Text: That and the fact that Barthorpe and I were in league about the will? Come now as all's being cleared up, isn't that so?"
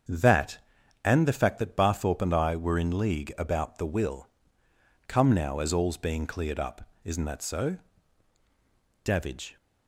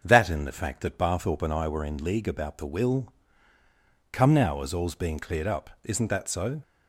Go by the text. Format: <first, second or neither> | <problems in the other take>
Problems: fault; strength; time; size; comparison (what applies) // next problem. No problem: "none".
second | starts louder than the rest; strong; until 1.5 s; 7.5 dB; also in the second // goes on to say "Davidge"; from 9.0 s on; 0.54 s long